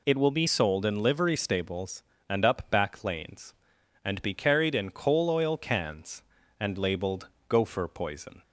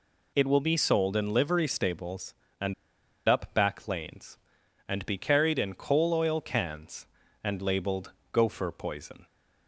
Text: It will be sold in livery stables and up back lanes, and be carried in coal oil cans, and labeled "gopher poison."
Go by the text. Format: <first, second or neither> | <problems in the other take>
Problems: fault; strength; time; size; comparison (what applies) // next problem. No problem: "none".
first | pauses between "and" and "up"; noticeable; at 2.7 s; 0.55 s long // pauses between "labeled" and "gopher"; slight; at 8.1 s; 0.22 s long; slight in the first